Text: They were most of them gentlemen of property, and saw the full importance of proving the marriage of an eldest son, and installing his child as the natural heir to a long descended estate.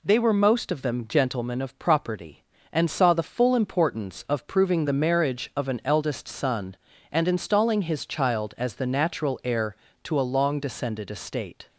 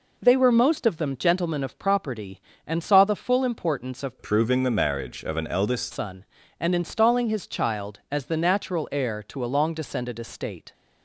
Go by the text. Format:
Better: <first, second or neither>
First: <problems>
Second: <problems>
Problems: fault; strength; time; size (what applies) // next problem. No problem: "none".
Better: first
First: none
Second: changes voice from "proving" to "eldest"; from 4.2 to 5.9 s; 1.7 s long